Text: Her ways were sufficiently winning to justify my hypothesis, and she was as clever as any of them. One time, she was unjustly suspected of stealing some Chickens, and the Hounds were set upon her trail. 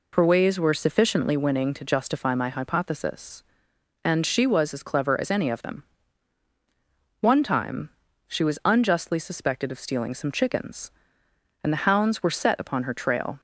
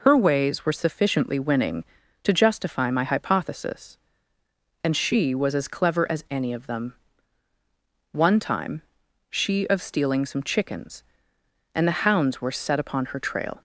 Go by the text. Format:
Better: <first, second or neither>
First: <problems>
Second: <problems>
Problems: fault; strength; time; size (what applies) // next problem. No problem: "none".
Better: first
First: none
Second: skips "was unjustly suspected"; at 9.6 s